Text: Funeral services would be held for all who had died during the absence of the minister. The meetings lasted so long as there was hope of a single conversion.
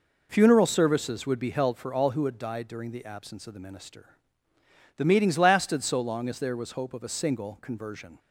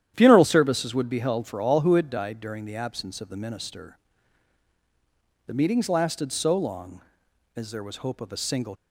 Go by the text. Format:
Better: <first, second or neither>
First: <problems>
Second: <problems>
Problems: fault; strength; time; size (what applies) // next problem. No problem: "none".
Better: first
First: none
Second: starts louder than the rest; strong; until 1.1 s; 10.5 dB // stops before "conversion"; at 8.7 s